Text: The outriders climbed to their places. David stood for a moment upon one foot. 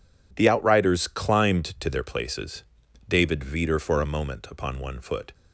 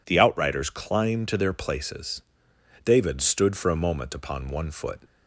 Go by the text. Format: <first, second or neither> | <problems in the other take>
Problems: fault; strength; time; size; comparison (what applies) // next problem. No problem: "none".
second | says "veter" for "stood"; at 3.4 s